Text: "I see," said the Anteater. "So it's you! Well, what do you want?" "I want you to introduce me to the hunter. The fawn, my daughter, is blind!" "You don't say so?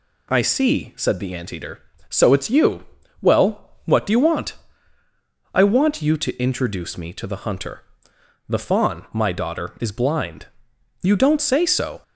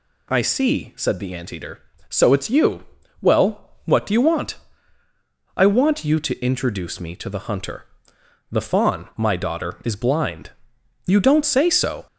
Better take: first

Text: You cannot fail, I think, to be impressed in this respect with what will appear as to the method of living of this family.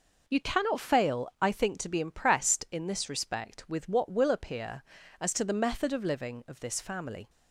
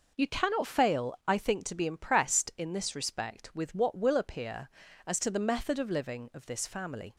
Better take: neither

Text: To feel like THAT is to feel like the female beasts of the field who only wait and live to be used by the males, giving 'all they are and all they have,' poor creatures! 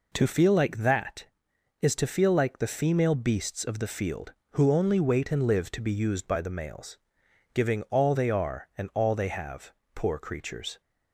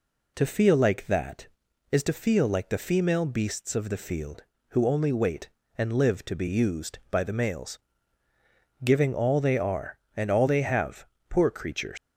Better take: first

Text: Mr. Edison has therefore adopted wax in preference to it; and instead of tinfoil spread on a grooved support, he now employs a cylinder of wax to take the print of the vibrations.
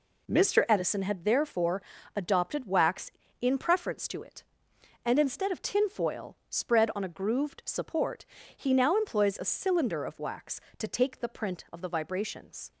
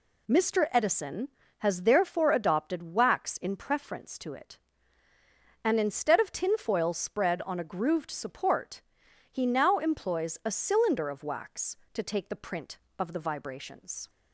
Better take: second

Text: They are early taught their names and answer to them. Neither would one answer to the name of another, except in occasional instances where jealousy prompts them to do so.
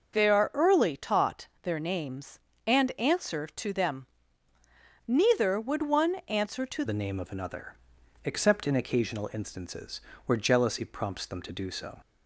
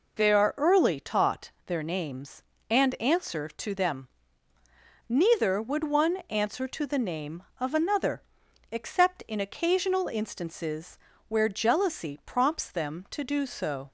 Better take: second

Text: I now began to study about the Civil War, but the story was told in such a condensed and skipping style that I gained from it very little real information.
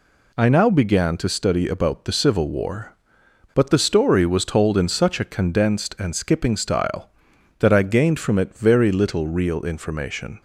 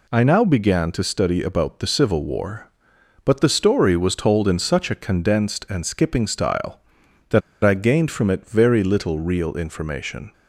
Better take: first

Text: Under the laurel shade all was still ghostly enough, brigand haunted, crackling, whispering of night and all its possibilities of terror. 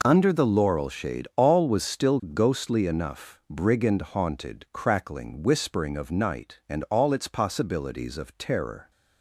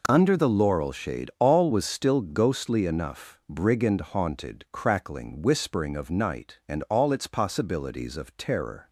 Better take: neither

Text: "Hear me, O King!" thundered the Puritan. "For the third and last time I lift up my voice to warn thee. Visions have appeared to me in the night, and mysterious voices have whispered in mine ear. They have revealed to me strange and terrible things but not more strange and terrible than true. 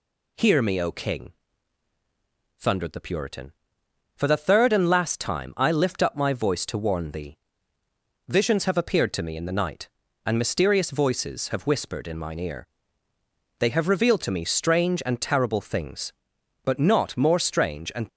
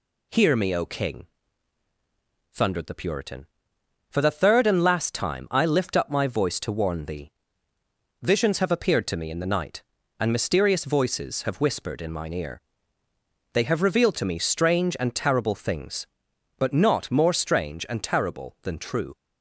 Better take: second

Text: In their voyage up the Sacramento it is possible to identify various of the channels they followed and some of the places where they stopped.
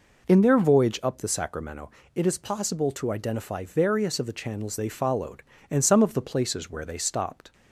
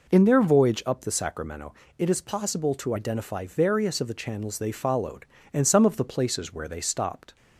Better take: neither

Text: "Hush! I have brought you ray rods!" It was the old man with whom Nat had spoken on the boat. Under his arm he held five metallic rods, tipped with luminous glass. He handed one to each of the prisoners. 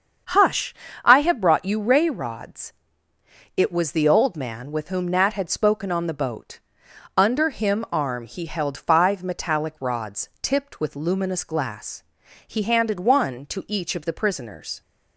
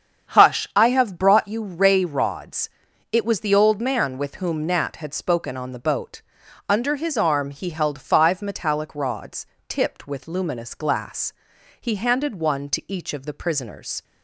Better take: second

